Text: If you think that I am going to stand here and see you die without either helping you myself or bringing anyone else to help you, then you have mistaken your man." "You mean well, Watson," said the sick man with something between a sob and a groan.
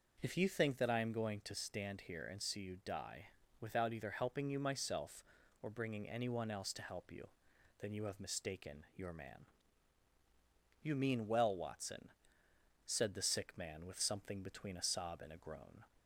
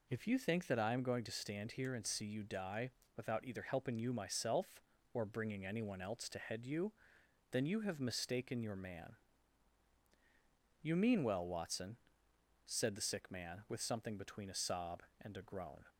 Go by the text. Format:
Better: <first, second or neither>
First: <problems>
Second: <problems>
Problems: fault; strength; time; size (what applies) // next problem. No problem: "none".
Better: first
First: pauses between "die" and "without"; slight; at 3.2 s; 0.34 s long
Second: pauses between "die" and "without"; slight; at 2.9 s; 0.24 s long // says "head" for "help"; at 6.3 s